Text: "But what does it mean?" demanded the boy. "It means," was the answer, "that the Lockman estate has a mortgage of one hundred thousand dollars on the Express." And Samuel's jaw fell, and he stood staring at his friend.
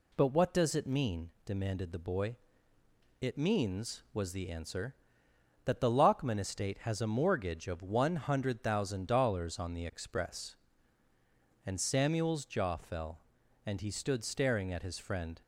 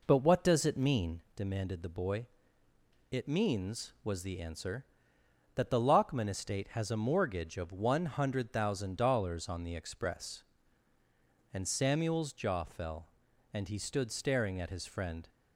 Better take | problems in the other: first | starts louder than the rest; noticeable; until 1.4 s; 4 dB

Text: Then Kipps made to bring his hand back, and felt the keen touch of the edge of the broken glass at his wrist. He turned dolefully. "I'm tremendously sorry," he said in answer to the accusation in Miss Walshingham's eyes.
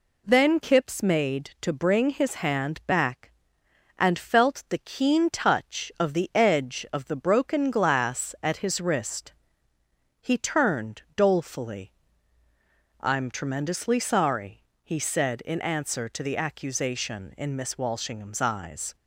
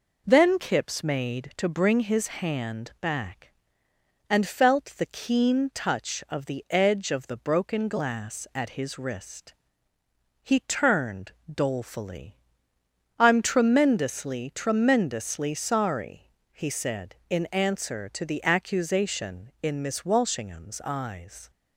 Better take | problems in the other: first | pauses between "turned" and "dolefully"; slight; at 11.3 s; 0.22 s long // says "tremendously" twice; at 14.5 s

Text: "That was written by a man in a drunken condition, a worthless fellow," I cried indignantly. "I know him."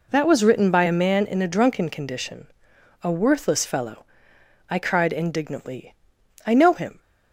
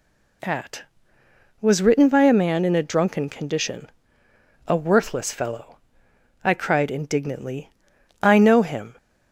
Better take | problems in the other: first | says "At" for "That"; at 0.4 s

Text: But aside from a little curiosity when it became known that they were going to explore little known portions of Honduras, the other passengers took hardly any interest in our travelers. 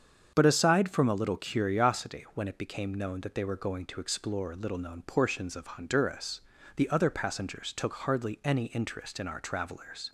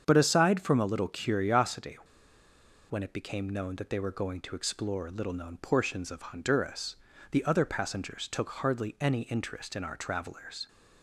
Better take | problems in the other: first | starts louder than the rest; strong; until 1.0 s; 7.5 dB; strong in the first // pauses between "curiosity" and "when"; noticeable; at 1.9 s; 0.90 s long

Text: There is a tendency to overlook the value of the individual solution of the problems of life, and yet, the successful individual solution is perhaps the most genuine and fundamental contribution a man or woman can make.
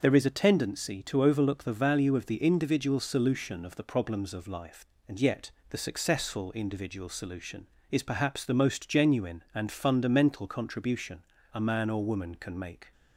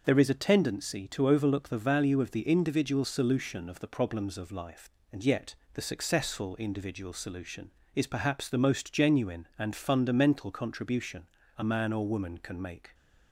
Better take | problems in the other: neither | pauses between "contribution" and "a"; slight; the same in both

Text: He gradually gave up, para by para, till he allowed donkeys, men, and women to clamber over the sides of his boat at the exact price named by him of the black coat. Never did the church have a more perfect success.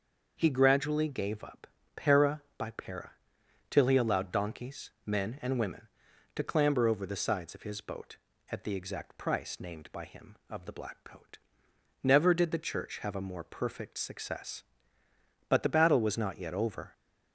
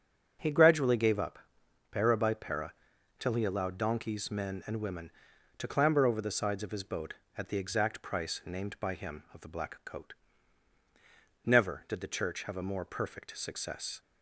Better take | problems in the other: second | starts louder than the rest; until 1.3 s; 6 dB; also in the second // goes on to say "But the battle was not yet over"; from 15.4 s on; 1.4 s long

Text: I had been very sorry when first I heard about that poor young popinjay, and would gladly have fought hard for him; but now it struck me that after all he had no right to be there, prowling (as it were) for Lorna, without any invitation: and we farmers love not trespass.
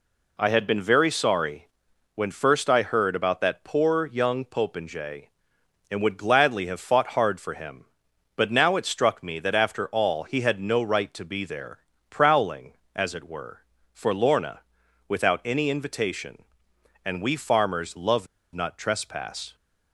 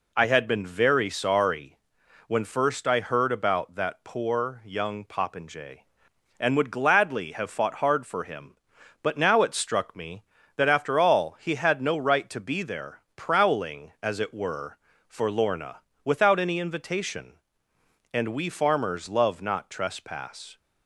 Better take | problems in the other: second | pauses between "sorry" and "when"; noticeable; at 1.6 s; 0.46 s long; noticeable in the second // pauses between "love" and "not"; slight; at 18.2 s; 0.28 s long

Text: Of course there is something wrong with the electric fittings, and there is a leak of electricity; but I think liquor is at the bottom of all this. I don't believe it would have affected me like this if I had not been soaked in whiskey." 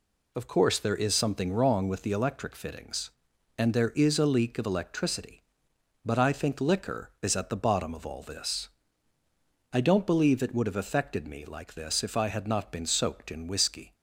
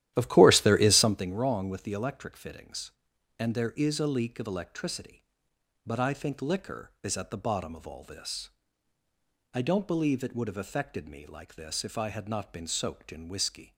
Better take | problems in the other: first | starts louder than the rest; strong; until 1.3 s; 13 dB

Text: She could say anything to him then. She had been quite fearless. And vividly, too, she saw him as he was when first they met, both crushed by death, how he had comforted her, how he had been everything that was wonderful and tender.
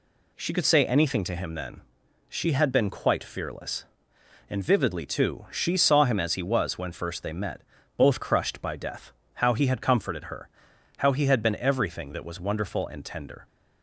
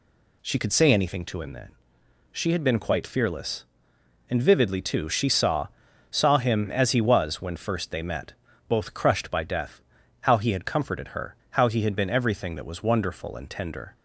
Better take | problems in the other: first | says "saw" twice; at 6.1 s

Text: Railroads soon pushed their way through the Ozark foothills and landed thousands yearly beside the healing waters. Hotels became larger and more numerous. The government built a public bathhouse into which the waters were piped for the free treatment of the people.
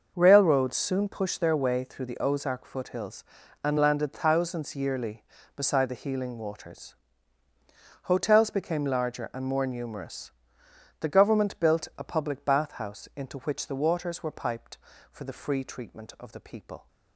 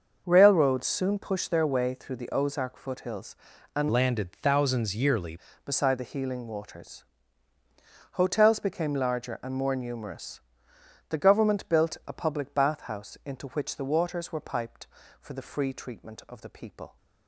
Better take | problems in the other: first | starts louder than the rest; until 1.2 s; 6 dB; noticeable in the first // changes voice from "landed" to "yearly"; from 3.9 to 5.3 s; 1.4 s long

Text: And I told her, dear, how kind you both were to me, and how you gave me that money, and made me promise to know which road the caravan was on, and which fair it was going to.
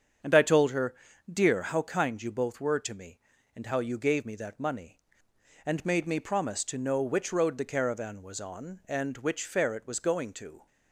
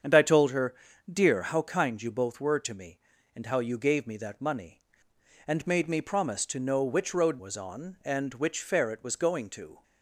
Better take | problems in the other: first | starts louder than the rest; strong; until 1.4 s; 7.5 dB; strong in the first // skips "the caravan"; at 7.3 s

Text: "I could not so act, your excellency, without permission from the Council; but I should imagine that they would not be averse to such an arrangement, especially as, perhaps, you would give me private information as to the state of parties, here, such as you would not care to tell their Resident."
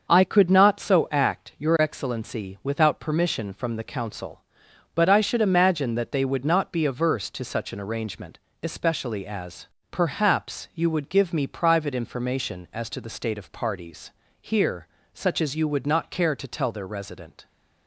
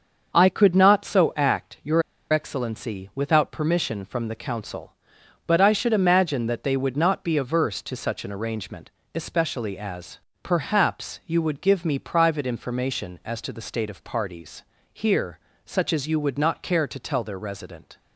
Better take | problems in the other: first | starts louder than the rest; until 1.3 s; 6.5 dB; also in the first // pauses between "your" and "excellency"; slight; at 2.0 s; 0.29 s long

